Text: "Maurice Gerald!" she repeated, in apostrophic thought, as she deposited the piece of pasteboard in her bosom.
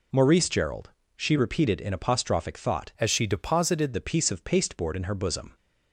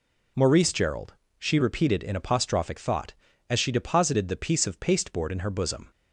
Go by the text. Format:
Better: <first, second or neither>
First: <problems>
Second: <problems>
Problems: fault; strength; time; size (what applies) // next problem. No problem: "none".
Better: second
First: changes voice from "as" to "deposited"; from 2.9 to 3.9 s; 1.0 s long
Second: none